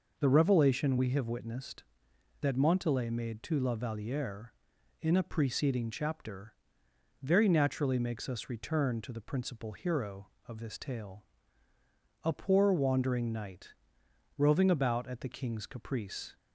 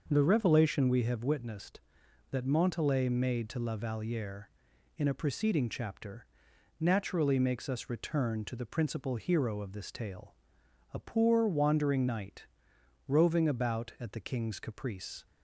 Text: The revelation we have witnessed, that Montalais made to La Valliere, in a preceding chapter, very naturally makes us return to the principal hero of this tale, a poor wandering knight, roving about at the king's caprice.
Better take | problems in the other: first | skips "very"; at 6.5 s

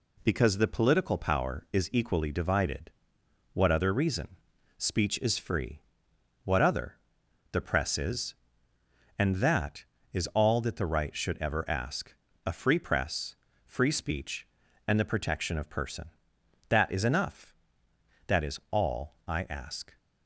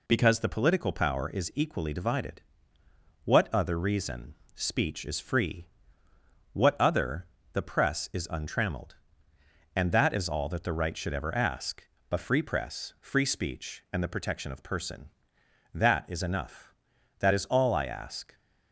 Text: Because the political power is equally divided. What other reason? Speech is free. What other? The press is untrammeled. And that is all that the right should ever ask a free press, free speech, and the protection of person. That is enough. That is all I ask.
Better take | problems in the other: second | skips "untrammeled"; at 8.7 s // pauses between "ask" and "a"; slight; at 12.1 s; 0.32 s long; slight in the second

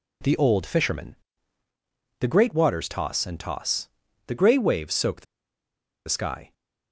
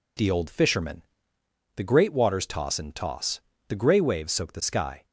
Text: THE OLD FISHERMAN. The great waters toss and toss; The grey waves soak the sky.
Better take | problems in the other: second | pauses between "the" and "sky"; noticeable; at 5.2 s; 0.83 s long

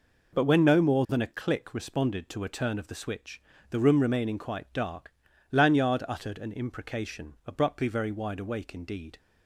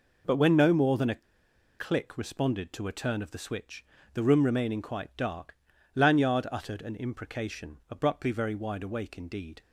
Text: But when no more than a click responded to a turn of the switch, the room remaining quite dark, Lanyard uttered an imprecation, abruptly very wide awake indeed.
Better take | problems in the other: first | pauses between "a" and "click"; noticeable; at 1.2 s; 0.57 s long

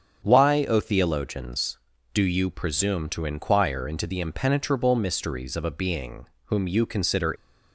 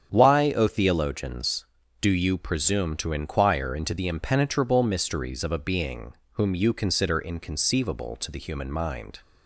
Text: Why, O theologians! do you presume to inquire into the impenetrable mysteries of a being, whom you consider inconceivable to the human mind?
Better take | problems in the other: second | starts louder than the rest; strong; until 1.3 s; 7.5 dB; strong in the second // stops before "inconceivable to the human mind"; at 7.3 s

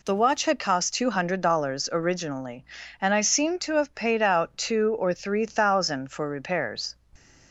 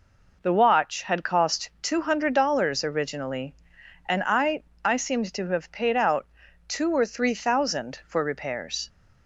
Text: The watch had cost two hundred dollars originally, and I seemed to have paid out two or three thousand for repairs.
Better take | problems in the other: first | says "I" twice; at 4.8 s // pauses between "out" and "two"; at 6.2 s; 0.42 s long

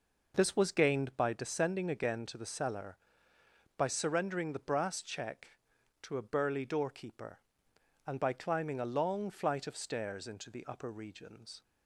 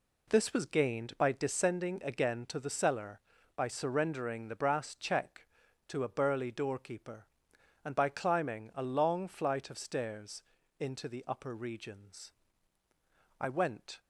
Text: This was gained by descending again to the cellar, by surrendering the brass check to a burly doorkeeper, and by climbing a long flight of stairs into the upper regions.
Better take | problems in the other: first | pauses between "stairs" and "into"; at 10.4 s; 0.38 s long // goes on to say "I went"; noticeable; from 13.3 s on; 0.62 s long

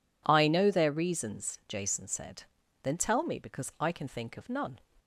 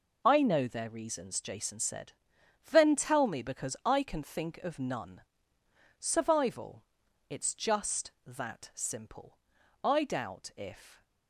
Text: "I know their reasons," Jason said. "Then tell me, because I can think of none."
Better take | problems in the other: first | goes on to say "Survival it's just that simple I doubt if"; strong; from 5.9 s on; 5.0 s long

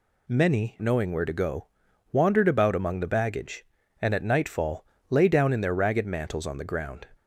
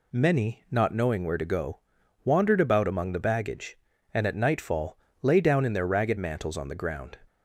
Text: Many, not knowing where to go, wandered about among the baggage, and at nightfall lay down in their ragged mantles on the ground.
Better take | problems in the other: second | skips "not"; at 0.8 s // pauses between "nightfall" and "lay"; slight; at 4.8 s; 0.24 s long; slight in the second

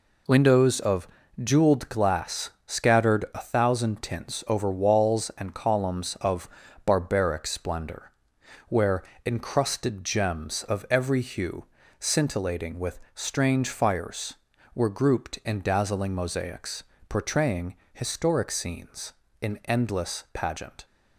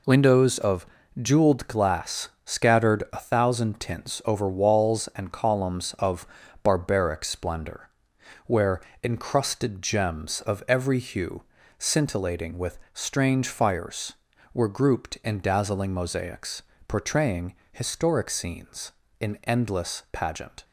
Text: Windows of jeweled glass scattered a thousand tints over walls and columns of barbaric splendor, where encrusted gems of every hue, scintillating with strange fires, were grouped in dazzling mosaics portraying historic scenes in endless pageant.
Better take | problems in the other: neither | pauses between "of" and "jeweled"; slight; the same in both // pauses between "glass" and "scattered"; slight; the same in both // pauses between "of" and "barbaric"; slight; the same in both // pauses between "where" and "encrusted"; slight; the same in both // pauses between "with" and "strange"; slight; the same in both // pauses between "mosaics" and "portraying"; slight; the same in both // pauses between "portraying" and "historic"; slight; the same in both

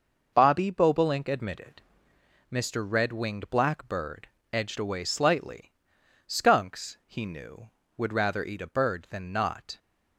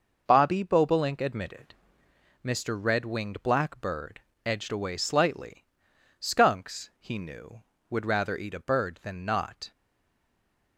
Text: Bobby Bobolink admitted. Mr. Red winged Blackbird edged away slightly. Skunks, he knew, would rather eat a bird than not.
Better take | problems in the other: first | pauses between "Blackbird" and "edged"; slight; at 4.1 s; 0.26 s long; slight in the first // stays silent after the last word; from 9.7 s on; 1.0 s long

